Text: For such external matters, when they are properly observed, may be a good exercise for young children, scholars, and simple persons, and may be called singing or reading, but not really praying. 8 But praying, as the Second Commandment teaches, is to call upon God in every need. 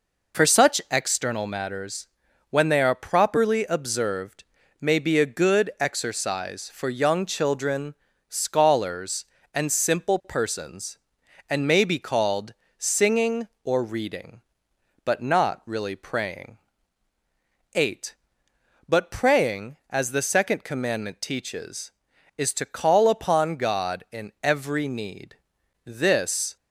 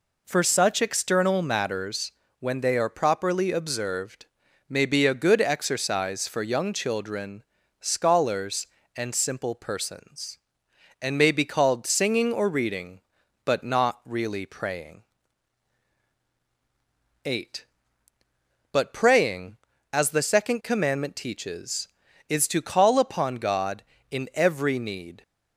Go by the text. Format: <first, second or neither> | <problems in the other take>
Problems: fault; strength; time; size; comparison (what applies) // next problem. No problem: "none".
second | pauses between "called" and "singing"; slight; at 12.5 s; 0.24 s long // goes on to say "This"; noticeable; from 25.8 s on; 0.72 s long